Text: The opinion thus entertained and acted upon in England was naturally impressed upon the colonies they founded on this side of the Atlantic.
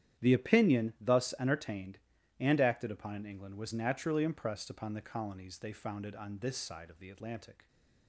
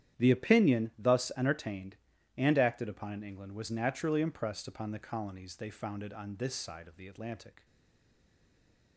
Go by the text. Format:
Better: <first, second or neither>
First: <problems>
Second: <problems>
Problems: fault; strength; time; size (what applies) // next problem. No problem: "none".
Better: first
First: starts louder than the rest; strong; until 1.2 s; 10.5 dB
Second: starts louder than the rest; strong; until 1.2 s; 10.5 dB // stays silent after the last word; noticeable; from 7.6 s on; 1.3 s long